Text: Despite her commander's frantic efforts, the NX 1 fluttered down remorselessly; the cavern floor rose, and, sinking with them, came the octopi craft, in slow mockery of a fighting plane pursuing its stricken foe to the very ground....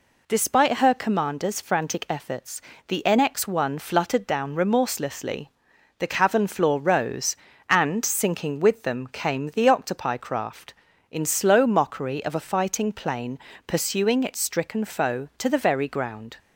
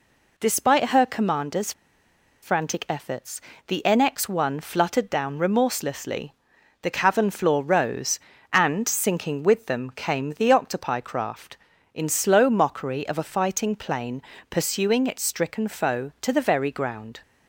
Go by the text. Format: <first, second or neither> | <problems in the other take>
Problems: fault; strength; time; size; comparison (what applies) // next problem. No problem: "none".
first | pauses between "commander's" and "frantic"; noticeable; at 1.7 s; 0.69 s long // pauses between "plane" and "pursuing"; slight; at 14.2 s; 0.26 s long; slight in the first